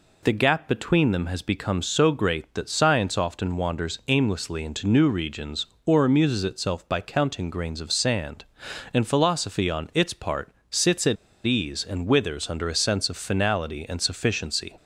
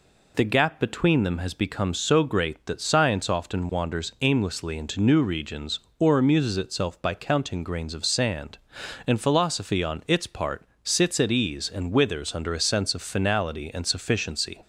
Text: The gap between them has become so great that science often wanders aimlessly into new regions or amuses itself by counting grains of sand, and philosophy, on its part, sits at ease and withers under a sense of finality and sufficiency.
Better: second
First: pauses between "at" and "ease"; slight; at 11.1 s; 0.30 s long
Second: none

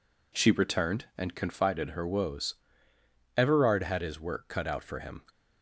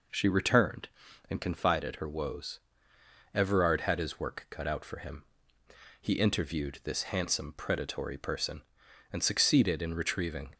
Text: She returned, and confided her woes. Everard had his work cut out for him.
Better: first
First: none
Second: goes on to say "He interviewed this handsome predatory person and succeeded in retrieving"; strong; from 6.0 s on; 4.5 s long

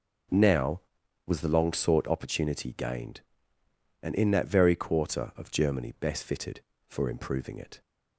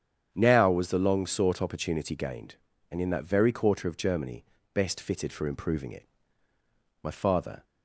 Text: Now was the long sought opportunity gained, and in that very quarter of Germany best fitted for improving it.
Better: first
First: none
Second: starts louder than the rest; strong; until 1.3 s; 8.5 dB // pauses between "Germany" and "best"; slight; at 4.4 s; 0.28 s long // goes on to say "My father"; from 7.0 s on; 0.60 s long

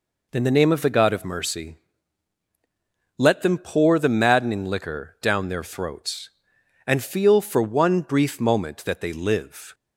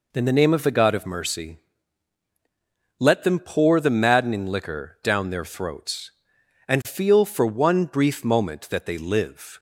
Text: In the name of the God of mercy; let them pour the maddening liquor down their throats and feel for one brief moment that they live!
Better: neither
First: none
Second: none

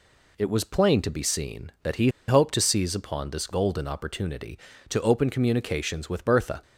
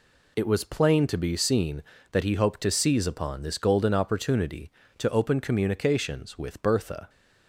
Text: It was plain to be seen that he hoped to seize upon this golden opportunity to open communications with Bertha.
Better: second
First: pauses between "he" and "hoped"; slight; at 2.0 s; 0.19 s long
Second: none

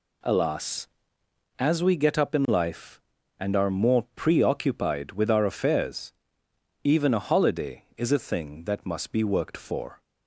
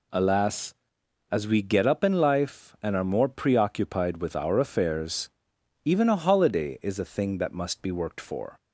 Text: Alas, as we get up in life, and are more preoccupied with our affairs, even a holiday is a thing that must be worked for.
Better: neither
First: none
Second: none

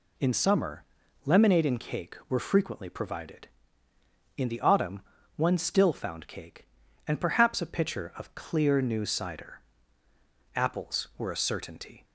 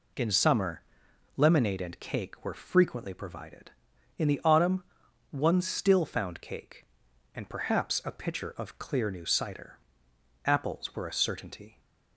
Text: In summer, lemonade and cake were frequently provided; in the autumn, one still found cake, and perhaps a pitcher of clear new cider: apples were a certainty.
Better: neither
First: none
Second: none

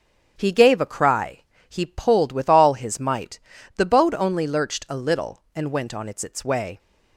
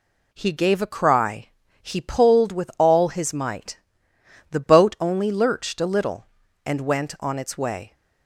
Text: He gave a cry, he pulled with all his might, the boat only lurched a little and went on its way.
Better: second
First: starts louder than the rest; strong; until 1.3 s; 7.5 dB // says "its" twice; at 6.2 s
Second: none

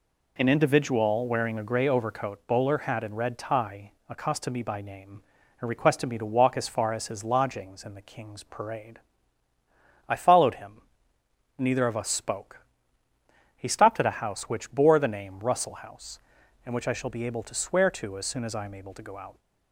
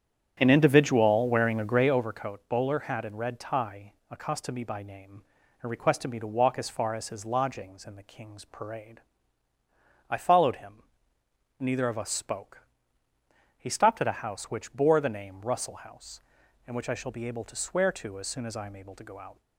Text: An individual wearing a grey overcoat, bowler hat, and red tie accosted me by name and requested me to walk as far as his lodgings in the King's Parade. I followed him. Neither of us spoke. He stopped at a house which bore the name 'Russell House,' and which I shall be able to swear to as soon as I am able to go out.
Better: first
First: pauses between "tie" and "accosted"; slight; at 3.9 s; 0.16 s long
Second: starts louder than the rest; strong; until 2.0 s; 9 dB // pauses between "tie" and "accosted"; slight; at 3.9 s; 0.16 s long

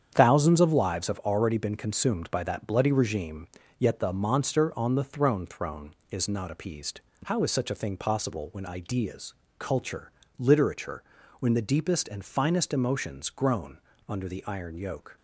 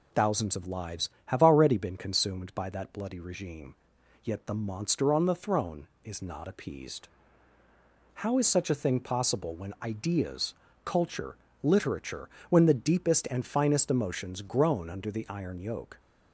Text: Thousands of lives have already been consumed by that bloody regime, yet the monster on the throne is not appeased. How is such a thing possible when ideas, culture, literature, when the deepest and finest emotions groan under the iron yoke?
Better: second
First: starts louder than the rest; strong; until 1.1 s; 8.5 dB // says "throne" twice; at 5.4 s // pauses between "groan" and "under"; slight; at 13.7 s; 0.28 s long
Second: none

